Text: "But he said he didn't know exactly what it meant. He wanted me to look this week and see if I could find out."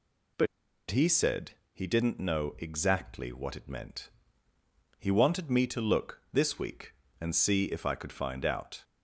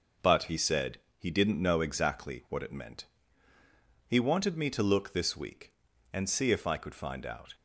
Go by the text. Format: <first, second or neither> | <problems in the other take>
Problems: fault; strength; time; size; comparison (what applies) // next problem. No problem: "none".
second | pauses between "But" and "he"; at 0.4 s; 0.44 s long // pauses between "said" and "he"; slight; at 1.5 s; 0.20 s long; slight in the second